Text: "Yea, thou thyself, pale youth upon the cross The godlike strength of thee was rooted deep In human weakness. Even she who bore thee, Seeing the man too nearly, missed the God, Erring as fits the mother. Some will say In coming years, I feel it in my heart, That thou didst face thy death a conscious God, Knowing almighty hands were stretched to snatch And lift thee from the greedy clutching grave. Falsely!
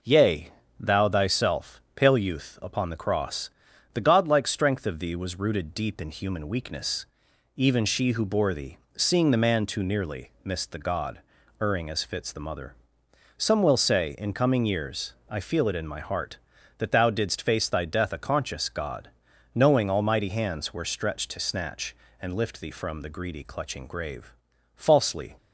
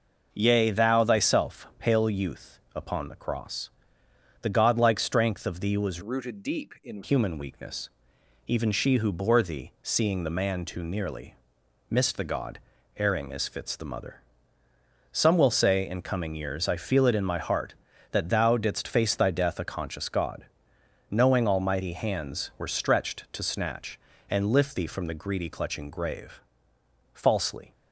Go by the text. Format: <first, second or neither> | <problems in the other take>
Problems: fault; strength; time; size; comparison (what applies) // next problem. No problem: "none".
first | pauses between "cross" and "The"; noticeable; at 3.6 s; 0.74 s long; also in the first // changes voice from "rooted" to "In"; from 6.0 to 7.0 s; 1.0 s long